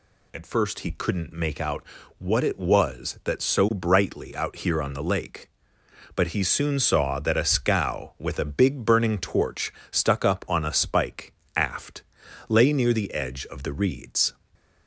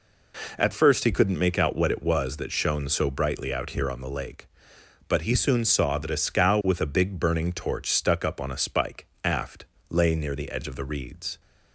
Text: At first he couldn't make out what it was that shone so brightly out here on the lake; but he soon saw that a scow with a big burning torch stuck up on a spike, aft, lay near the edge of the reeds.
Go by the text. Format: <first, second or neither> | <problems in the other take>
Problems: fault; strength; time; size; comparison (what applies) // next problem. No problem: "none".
second | pauses between "out" and "what"; slight; at 1.8 s; 0.34 s long // skips "shone"; at 3.4 s // pauses between "torch" and "stuck"; slight; at 9.7 s; 0.18 s long